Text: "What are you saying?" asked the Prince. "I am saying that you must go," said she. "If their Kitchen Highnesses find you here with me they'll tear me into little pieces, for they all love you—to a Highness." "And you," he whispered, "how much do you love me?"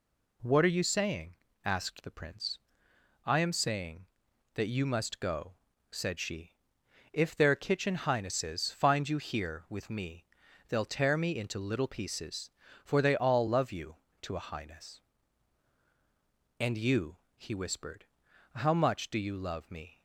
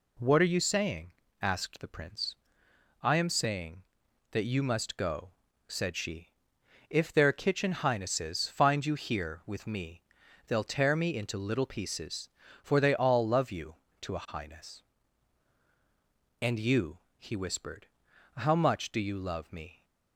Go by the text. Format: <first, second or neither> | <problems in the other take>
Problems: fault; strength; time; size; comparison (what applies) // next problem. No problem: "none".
neither | pauses between "me" and "they'll"; the same in both